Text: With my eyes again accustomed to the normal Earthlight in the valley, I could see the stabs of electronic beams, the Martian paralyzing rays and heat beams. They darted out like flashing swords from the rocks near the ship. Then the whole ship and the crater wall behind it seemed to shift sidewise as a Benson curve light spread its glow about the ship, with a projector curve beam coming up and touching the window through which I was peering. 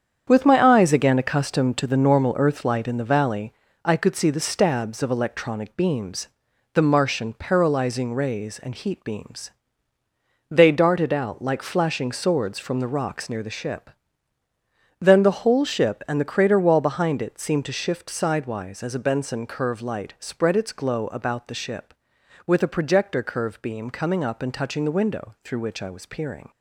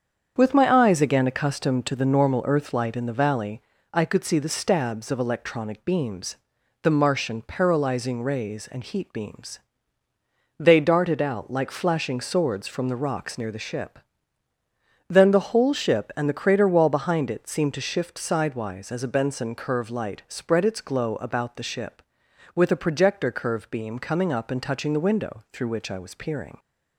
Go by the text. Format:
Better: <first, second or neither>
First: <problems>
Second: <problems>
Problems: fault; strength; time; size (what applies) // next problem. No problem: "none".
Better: second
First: gets quieter; strong; throughout; 8 dB // starts louder than the rest; strong; until 1.2 s; 8 dB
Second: starts louder than the rest; strong; until 1.3 s; 7.5 dB